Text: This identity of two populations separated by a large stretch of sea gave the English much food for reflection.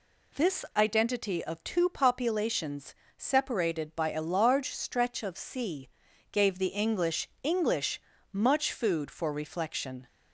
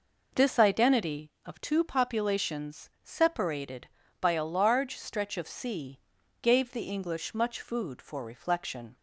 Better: second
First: pauses between "populations" and "separated"; slight; at 2.9 s; 0.22 s long // pauses between "sea" and "gave"; at 5.8 s; 0.42 s long // says "English" twice; at 7.4 s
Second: pauses between "sea" and "gave"; at 5.9 s; 0.42 s long

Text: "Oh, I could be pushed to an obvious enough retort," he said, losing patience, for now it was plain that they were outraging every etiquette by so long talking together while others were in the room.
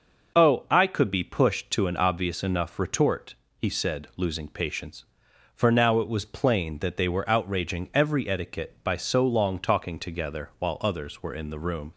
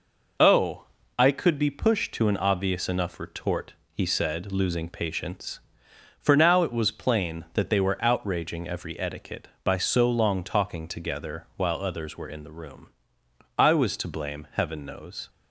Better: first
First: none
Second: goes on to say "I was to blame Heaven knows"; strong; from 13.5 s on; 1.7 s long

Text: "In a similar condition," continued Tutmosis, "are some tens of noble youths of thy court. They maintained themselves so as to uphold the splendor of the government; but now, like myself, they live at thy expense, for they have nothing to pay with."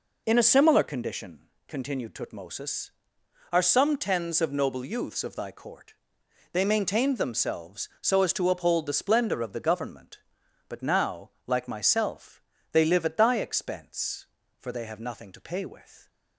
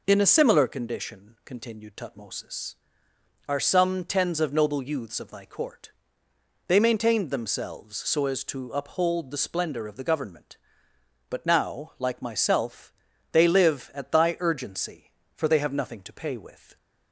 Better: first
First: none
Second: says "urgency" for "expense"; at 14.4 s

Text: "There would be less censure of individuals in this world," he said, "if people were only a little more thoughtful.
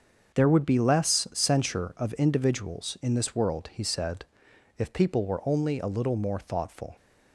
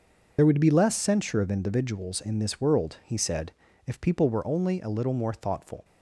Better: first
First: starts louder than the rest; until 1.4 s; 6.5 dB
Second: loses the start of "There"; at 0.3 s; 40 ms // starts louder than the rest; noticeable; until 1.3 s; 6 dB

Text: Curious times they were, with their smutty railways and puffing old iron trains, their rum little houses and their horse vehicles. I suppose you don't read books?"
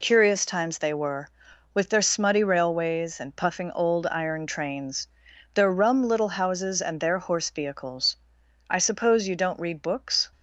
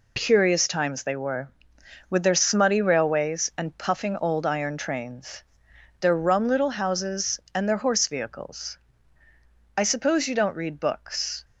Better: neither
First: none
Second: none

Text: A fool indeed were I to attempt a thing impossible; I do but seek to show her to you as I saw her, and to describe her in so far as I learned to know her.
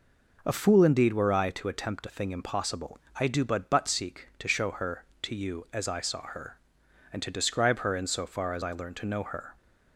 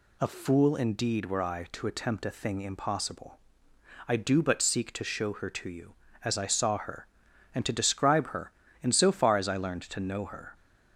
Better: second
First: says "but" twice; at 3.6 s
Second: none

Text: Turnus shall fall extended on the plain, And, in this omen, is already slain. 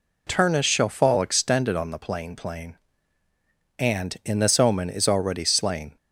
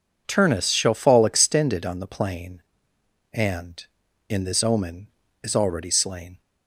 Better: second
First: says "plain" twice; at 2.3 s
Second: none

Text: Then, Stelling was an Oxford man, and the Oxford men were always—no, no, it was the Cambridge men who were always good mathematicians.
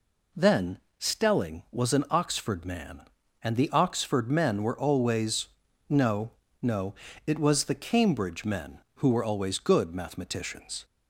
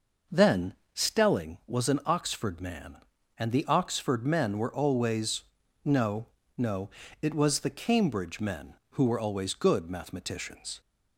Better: first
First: none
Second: starts louder than the rest; noticeable; until 1.5 s; 5.5 dB

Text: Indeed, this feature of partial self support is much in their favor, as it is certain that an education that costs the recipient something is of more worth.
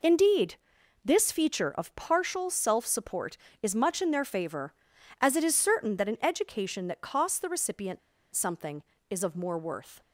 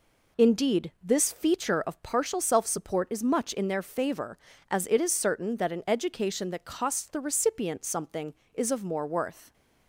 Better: second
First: pauses between "recipient" and "something"; slight; at 7.9 s; 0.35 s long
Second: none

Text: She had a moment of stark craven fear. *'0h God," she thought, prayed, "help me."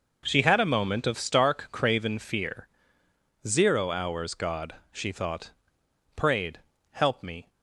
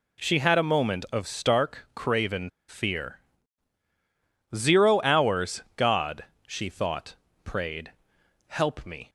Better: first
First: none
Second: pauses between "craven" and "fear"; slight; at 2.4 s; 0.19 s long

